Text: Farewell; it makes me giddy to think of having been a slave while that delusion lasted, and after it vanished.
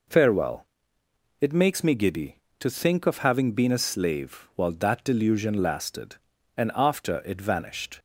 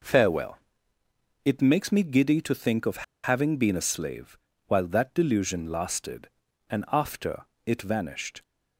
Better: first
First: none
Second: pauses between "of" and "having"; slight; at 3.0 s; 0.21 s long // pauses between "slave" and "while"; slight; at 4.3 s; 0.30 s long // pauses between "after" and "it"; slight; at 7.4 s; 0.22 s long

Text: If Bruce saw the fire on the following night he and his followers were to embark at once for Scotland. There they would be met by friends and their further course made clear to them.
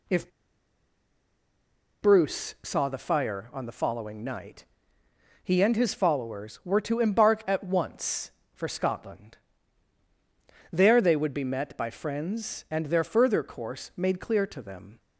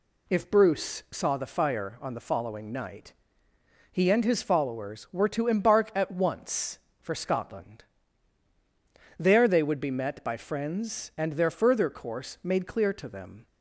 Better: second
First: pauses between "If" and "Bruce"; strong; at 0.2 s; 1.7 s long // pauses between "night" and "he"; noticeable; at 4.6 s; 0.80 s long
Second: pauses between "night" and "he"; noticeable; at 3.1 s; 0.80 s long

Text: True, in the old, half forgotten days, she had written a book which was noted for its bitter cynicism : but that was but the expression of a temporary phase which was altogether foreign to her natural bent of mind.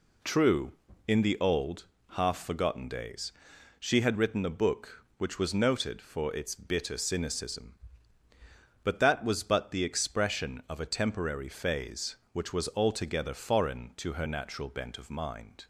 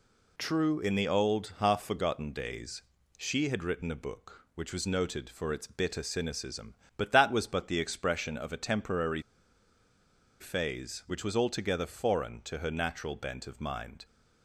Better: first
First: none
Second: pauses between "temporary" and "phase"; at 9.2 s; 1.1 s long

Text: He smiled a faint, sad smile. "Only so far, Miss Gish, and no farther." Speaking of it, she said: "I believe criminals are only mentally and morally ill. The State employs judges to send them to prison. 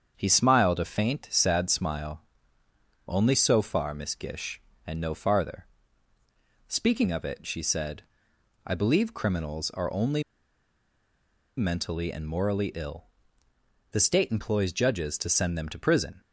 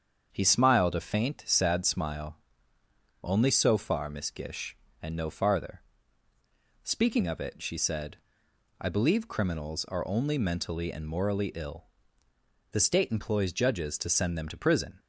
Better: second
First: starts louder than the rest; strong; until 1.1 s; 7.5 dB // pauses between "only" and "mentally"; strong; at 10.2 s; 1.3 s long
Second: starts louder than the rest; strong; until 1.3 s; 7.5 dB

